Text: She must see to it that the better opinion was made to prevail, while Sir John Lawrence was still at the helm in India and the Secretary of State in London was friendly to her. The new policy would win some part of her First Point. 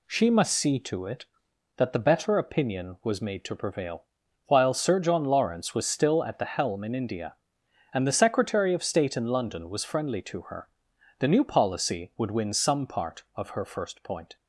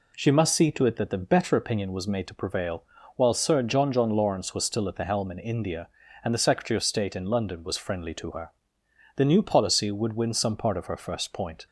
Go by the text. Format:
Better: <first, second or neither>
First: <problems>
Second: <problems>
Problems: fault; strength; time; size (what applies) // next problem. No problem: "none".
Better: first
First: none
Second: says "John" twice; at 3.9 s